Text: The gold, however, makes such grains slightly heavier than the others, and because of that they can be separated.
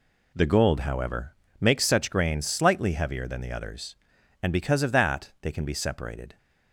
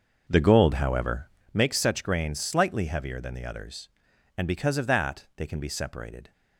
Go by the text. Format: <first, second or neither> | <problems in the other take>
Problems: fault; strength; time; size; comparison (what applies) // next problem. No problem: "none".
first | starts louder than the rest; until 1.5 s; 6 dB